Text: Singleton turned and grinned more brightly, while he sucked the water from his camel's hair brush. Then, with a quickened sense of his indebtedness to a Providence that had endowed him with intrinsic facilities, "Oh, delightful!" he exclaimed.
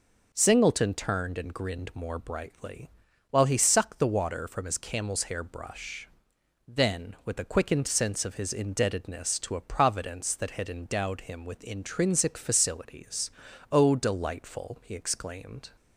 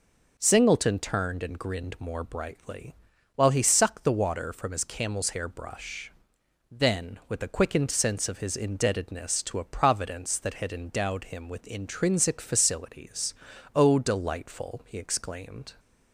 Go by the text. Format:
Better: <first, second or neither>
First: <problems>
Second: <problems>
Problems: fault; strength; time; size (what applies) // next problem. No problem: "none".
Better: neither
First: none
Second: none